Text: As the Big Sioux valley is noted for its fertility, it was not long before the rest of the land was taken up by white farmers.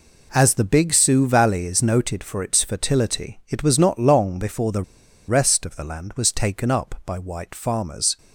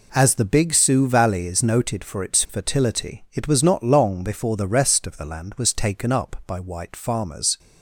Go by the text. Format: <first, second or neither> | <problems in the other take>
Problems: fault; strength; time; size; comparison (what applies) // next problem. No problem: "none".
second | pauses between "the" and "rest"; at 4.8 s; 0.44 s long